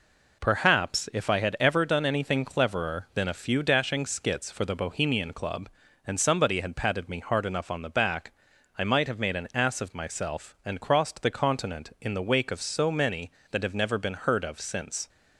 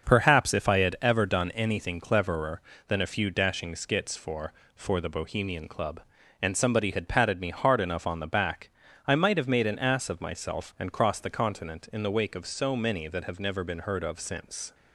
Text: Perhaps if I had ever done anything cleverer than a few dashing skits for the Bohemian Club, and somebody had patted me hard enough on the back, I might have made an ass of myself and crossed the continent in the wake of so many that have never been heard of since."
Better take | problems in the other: first | starts louder than the rest; until 1.0 s; 6.5 dB // says "for" twice; at 4.7 s

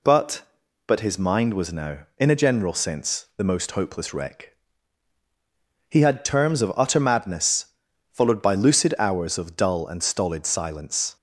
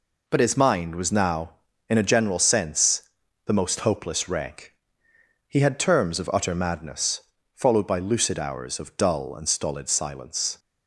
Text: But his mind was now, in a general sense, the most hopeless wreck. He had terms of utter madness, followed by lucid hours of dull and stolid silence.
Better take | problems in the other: second | says "But" twice; at 0.8 s

